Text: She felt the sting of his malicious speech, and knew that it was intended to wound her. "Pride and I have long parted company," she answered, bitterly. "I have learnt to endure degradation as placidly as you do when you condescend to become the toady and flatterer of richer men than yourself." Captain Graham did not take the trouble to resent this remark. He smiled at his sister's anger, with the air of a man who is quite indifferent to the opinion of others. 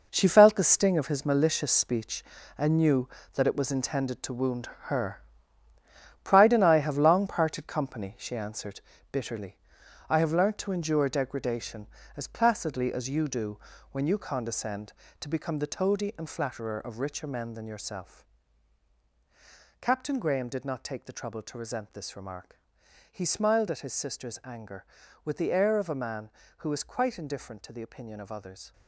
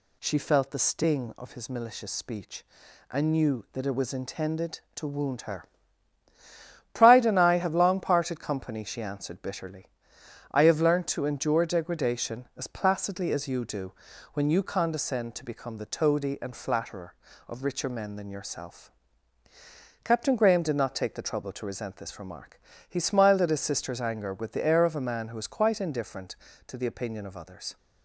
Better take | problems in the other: second | gets quieter; strong; throughout; 10.5 dB // pauses between "wound" and "her"; slight; at 4.6 s; 0.16 s long // pauses between "do" and "when"; slight; at 13.6 s; 0.32 s long; also in the second

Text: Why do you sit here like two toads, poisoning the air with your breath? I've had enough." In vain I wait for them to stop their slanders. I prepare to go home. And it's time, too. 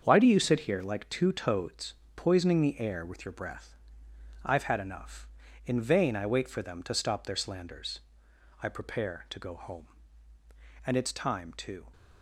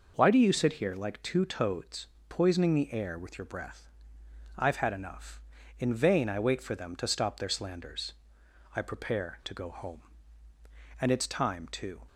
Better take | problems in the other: second | gets quieter; strong; throughout; 8.5 dB

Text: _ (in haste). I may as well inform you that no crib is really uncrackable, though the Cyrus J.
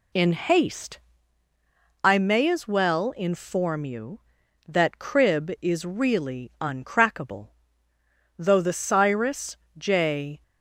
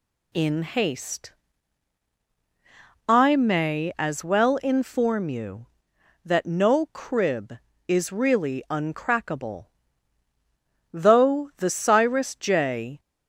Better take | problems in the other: second | skips "no"; at 4.9 s // pauses between "Cyrus" and "J"; slight; at 9.5 s; 0.22 s long

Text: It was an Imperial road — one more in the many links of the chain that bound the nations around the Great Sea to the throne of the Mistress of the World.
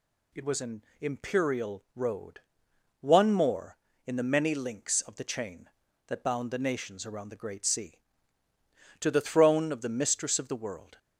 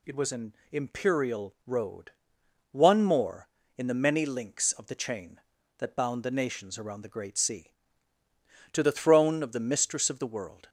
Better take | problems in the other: neither | pauses between "an" and "Imperial"; slight; the same in both

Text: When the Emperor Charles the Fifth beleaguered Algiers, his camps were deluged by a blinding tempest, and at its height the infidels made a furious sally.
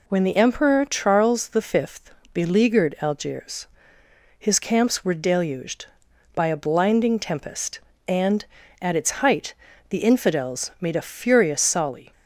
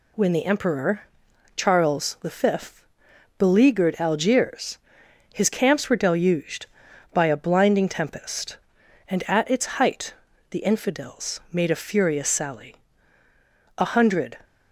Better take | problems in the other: first | pauses between "Emperor" and "Charles"; noticeable; at 1.0 s; 0.56 s long // pauses between "Fifth" and "beleaguered"; noticeable; at 2.8 s; 0.52 s long; slight in the first // pauses between "height" and "the"; slight; at 10.1 s; 0.36 s long; slight in the first // goes on to say "A hundred"; noticeable; from 13.7 s on; 0.62 s long

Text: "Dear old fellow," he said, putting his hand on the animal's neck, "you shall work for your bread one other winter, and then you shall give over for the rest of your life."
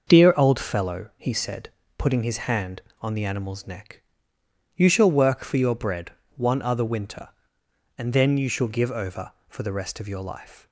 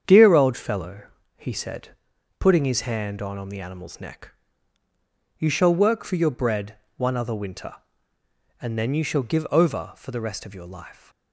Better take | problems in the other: first | starts louder than the rest; strong; until 1.3 s; 8 dB; noticeable in the first // says "on" twice; at 3.3 s // pauses between "bread" and "one"; slight; at 6.7 s; 0.22 s long; slight in the first

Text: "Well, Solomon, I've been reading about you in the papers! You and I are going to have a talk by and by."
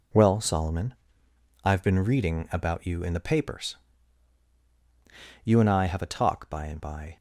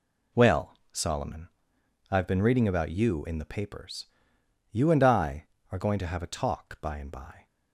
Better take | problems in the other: second | skips "are going to"; at 5.8 s

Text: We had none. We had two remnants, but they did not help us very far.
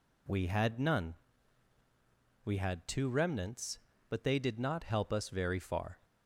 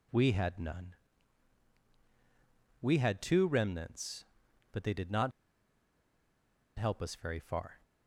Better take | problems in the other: first | pauses between "not" and "help"; strong; at 5.3 s; 1.4 s long

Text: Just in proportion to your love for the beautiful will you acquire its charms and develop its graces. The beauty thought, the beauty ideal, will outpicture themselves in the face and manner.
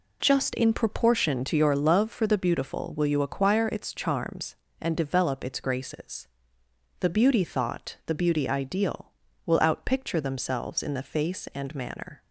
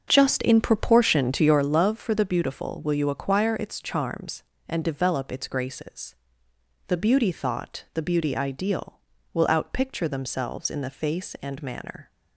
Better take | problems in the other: first | starts louder than the rest; until 1.7 s; 6.5 dB

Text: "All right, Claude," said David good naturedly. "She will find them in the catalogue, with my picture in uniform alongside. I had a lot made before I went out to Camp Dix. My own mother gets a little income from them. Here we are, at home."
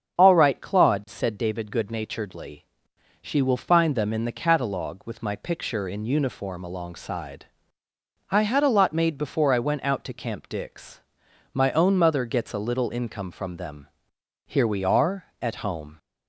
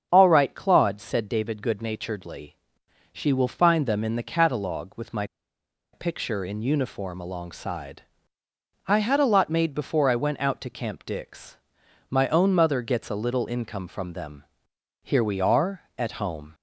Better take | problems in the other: first | starts louder than the rest; strong; until 1.1 s; 7 dB; strong in the first // pauses between "my" and "picture"; noticeable; at 5.2 s; 0.68 s long

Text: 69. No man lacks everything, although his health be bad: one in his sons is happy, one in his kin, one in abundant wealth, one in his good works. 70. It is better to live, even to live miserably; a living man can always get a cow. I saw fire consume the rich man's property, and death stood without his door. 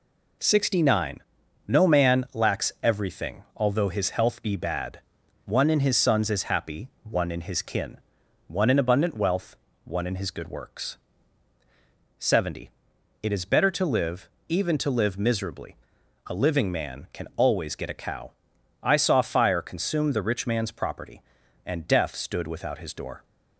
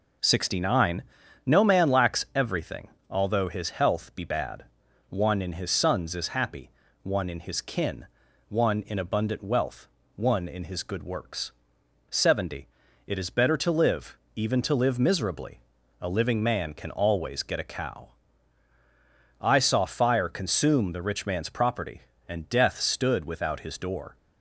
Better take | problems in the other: neither | none

